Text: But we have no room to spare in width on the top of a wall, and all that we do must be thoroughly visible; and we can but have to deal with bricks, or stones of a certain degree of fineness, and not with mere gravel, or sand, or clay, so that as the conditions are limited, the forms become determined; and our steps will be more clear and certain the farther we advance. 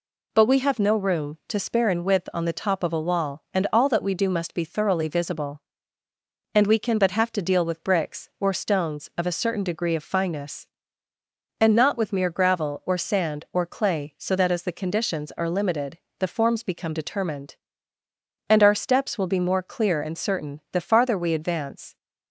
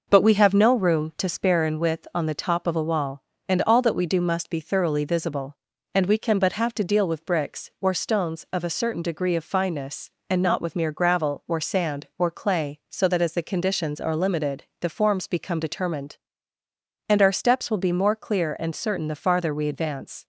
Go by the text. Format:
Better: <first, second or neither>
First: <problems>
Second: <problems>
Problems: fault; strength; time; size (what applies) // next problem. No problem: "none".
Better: first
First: none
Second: starts louder than the rest; noticeable; until 1.3 s; 5.5 dB